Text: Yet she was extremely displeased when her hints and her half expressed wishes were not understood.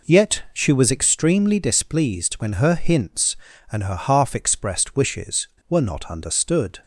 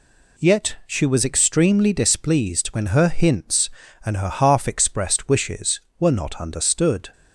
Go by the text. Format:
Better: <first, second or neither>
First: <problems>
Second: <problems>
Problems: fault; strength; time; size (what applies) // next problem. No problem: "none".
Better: second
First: starts louder than the rest; noticeable; until 1.1 s; 4.5 dB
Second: none